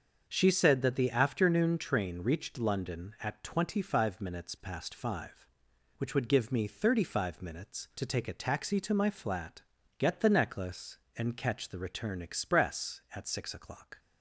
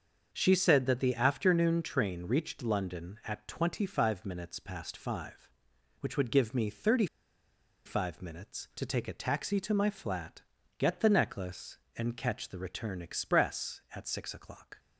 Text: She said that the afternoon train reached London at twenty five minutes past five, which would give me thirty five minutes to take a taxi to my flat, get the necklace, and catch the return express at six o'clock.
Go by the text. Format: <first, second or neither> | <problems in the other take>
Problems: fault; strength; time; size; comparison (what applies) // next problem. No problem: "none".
first | starts louder than the rest; until 1.3 s; 6.5 dB; also in the first // pauses between "thirty" and "five"; noticeable; at 7.0 s; 0.80 s long